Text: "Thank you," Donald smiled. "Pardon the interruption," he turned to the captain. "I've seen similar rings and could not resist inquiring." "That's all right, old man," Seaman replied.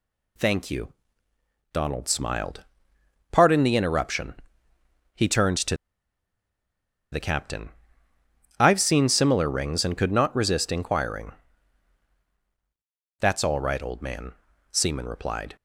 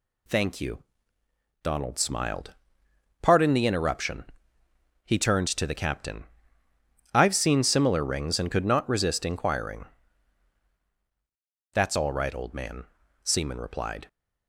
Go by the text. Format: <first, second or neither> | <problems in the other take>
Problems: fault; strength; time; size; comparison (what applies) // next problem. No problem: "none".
second | pauses between "to" and "the"; strong; at 5.7 s; 1.3 s long